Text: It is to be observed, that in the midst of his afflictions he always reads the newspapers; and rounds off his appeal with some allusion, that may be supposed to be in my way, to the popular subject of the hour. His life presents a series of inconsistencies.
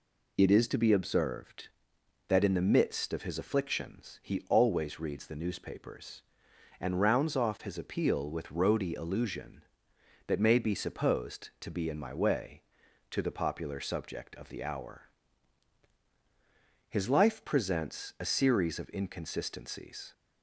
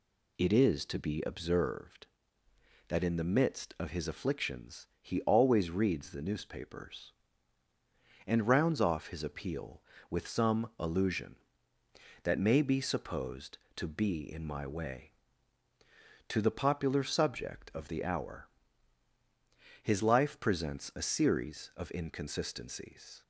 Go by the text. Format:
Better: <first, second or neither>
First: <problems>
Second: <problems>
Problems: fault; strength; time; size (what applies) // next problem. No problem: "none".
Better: second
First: says "roady" for "some"; at 8.5 s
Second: none